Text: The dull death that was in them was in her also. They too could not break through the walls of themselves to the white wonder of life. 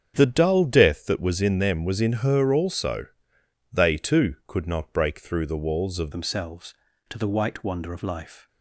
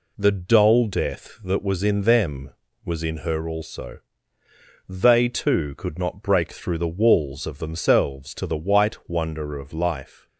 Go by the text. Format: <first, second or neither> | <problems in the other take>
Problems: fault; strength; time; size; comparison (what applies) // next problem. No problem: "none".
second | starts louder than the rest; strong; until 1.1 s; 8 dB // changes voice at "themselves"; from 6.1 s on; 2.3 s long